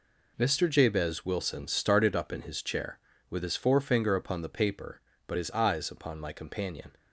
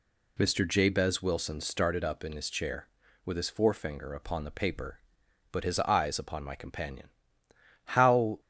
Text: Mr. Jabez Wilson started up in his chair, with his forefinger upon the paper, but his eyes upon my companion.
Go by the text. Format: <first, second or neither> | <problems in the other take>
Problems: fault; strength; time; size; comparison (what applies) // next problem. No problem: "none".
first | goes on to say "How"; from 7.8 s on; 0.56 s long